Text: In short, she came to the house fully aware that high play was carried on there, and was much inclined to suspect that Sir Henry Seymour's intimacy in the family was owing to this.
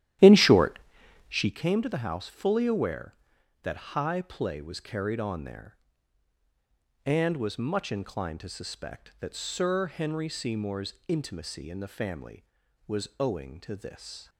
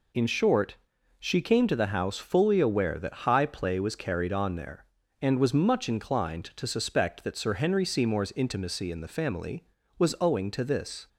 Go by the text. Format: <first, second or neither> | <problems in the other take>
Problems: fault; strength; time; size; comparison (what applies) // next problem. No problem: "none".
second | starts louder than the rest; strong; until 1.6 s; 12.5 dB